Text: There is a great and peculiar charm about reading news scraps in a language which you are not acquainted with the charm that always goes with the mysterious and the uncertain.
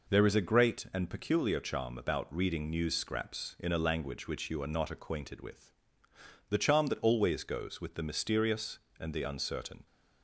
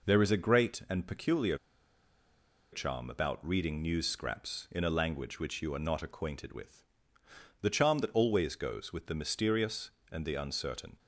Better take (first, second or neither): first